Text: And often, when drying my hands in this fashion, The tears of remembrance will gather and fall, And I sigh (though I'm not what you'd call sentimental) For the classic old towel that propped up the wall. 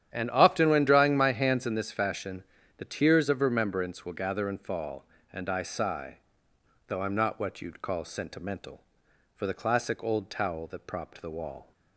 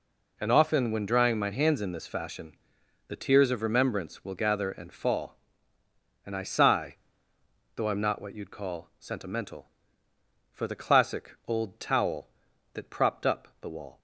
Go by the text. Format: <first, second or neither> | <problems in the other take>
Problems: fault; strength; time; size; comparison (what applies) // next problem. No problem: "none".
second | starts louder than the rest; strong; until 1.1 s; 10 dB // skips "up"; at 11.2 s